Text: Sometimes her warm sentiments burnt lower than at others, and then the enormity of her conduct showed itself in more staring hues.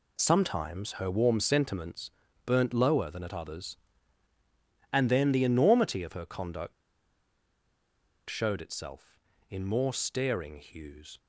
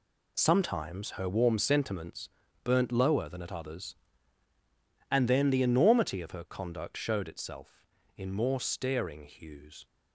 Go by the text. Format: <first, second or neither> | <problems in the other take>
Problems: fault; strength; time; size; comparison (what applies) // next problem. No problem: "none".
second | pauses between "sentiments" and "burnt"; slight; at 2.0 s; 0.36 s long; slight in the second // pauses between "conduct" and "showed"; strong; at 6.7 s; 1.5 s long